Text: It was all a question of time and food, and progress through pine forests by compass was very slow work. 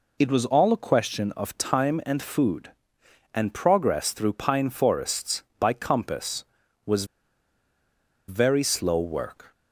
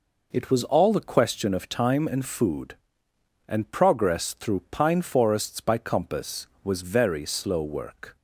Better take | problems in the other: second | pauses between "was" and "very"; at 7.0 s; 1.2 s long

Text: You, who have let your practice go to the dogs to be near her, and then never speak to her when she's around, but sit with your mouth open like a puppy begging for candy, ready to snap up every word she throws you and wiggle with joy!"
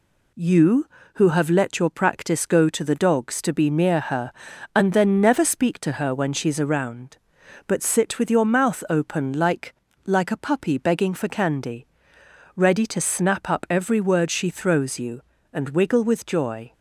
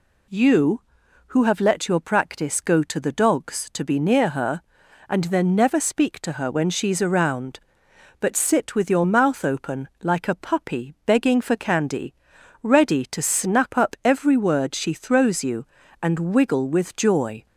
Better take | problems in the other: second | says "like" twice; at 10.0 s

